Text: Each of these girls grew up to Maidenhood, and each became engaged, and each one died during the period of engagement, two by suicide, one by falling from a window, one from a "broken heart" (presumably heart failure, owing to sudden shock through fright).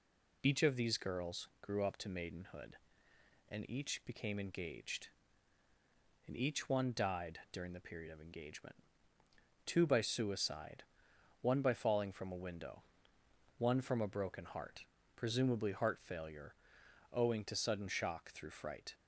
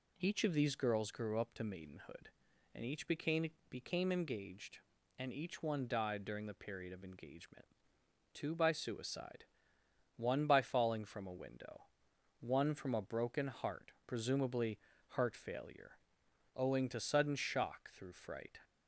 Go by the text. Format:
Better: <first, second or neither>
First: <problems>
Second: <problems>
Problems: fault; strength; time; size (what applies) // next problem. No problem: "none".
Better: first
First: none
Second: says "became" twice; at 3.6 s // pauses between "presumably" and "heart"; slight; at 14.7 s; 0.30 s long